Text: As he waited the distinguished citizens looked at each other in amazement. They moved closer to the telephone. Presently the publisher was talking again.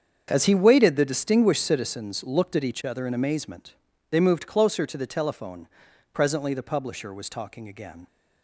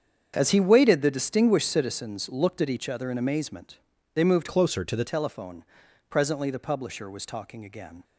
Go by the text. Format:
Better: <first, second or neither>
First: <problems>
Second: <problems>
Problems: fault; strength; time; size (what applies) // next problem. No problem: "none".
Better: first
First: starts louder than the rest; strong; until 1.2 s; 7.5 dB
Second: starts louder than the rest; strong; until 1.3 s; 7.5 dB // changes voice from "closer" to "the"; from 4.4 to 5.0 s; 0.6 s long